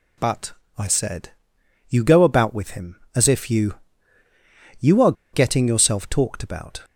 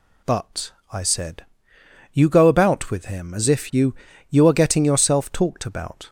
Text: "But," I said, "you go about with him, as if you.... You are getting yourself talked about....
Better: second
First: pauses between "are" and "getting"; slight; at 5.1 s; 0.20 s long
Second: none

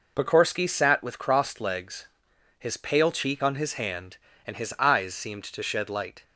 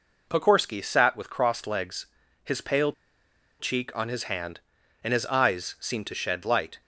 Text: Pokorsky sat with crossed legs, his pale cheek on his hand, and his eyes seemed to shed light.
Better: first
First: none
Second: pauses between "pale" and "cheek"; noticeable; at 2.9 s; 0.68 s long

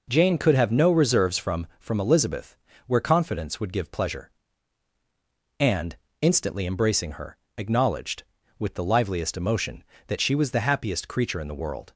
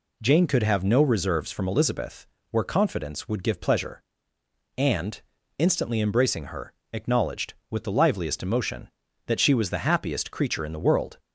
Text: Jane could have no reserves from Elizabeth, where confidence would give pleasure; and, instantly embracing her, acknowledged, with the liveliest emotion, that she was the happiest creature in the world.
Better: second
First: says "from" twice; at 1.7 s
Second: none

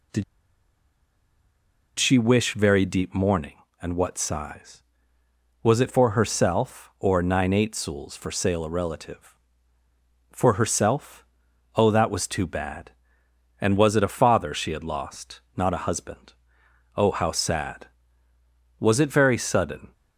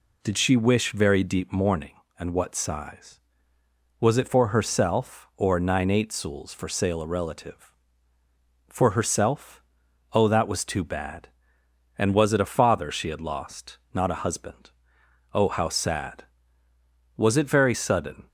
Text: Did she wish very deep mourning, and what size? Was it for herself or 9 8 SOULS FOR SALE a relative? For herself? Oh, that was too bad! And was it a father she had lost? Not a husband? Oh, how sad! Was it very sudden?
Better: second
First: pauses between "Did" and "she"; strong; at 0.2 s; 1.7 s long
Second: none

